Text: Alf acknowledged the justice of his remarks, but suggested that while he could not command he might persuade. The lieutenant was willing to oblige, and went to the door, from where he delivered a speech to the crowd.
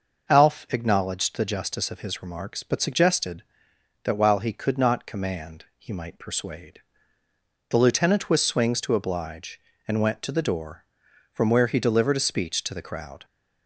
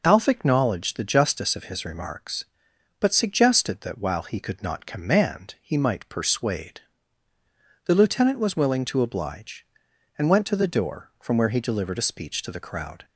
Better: second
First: says "swings" for "willing"; at 8.4 s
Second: none

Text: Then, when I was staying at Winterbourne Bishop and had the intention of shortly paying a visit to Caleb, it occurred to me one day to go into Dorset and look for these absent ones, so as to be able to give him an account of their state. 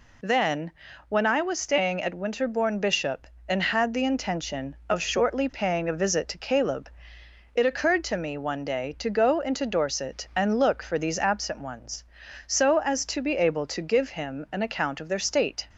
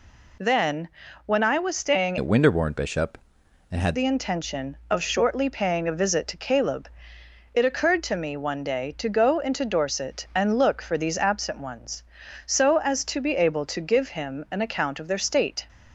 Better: first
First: none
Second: changes voice from "at" to "had"; from 2.1 to 3.9 s; 1.8 s long

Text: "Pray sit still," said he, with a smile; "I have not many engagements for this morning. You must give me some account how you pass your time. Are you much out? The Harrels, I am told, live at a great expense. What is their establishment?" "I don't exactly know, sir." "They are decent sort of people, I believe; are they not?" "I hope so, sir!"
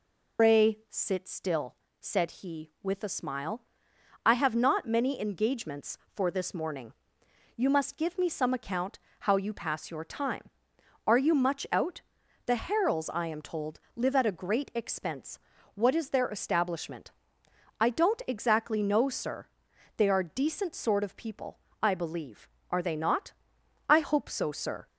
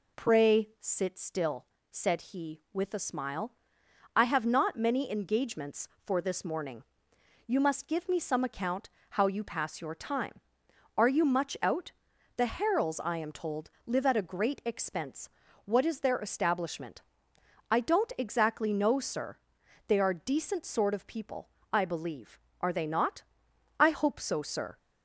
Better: second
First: loses the start of "Pray"; at 0.3 s; 150 ms // pauses between "account" and "how"; slight; at 8.9 s; 0.22 s long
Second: pauses between "account" and "how"; slight; at 8.8 s; 0.22 s long

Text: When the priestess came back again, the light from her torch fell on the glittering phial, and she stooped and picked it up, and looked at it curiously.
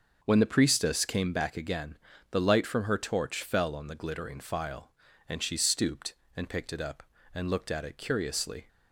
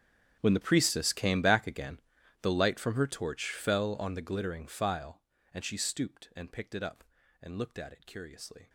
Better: first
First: starts louder than the rest; noticeable; until 1.2 s; 6 dB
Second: gets quieter; strong; throughout; 20 dB // starts louder than the rest; strong; until 1.4 s; 8.5 dB

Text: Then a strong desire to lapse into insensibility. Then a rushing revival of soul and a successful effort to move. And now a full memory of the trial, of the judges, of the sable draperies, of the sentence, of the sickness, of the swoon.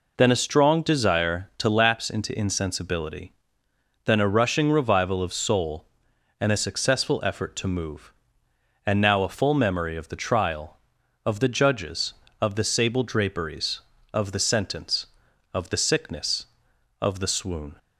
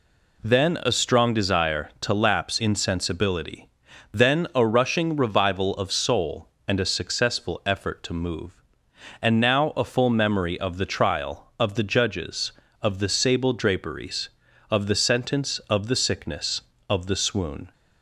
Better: first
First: none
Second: skips "into"; at 2.5 s

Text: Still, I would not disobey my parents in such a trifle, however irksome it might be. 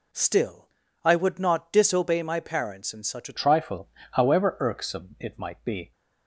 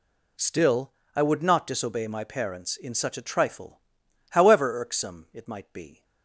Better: second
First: changes voice at "trifle"; from 3.3 s on; 2.6 s long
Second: none

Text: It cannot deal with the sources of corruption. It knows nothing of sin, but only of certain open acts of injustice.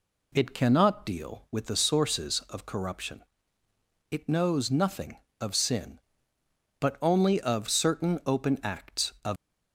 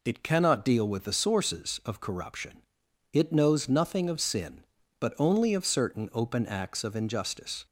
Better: second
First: stops before "injustice"; at 9.3 s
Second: none

